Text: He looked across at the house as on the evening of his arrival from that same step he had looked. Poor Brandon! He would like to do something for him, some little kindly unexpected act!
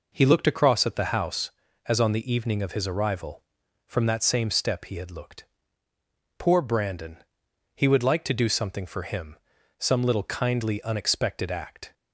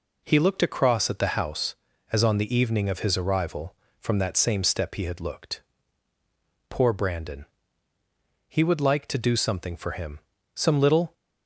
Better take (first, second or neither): first